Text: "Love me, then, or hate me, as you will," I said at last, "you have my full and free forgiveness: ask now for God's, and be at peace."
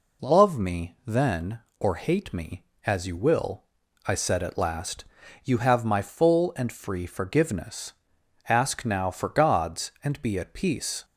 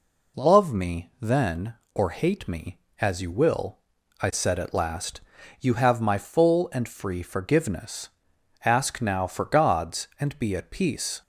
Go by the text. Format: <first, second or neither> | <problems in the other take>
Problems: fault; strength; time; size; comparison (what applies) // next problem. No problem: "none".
neither | none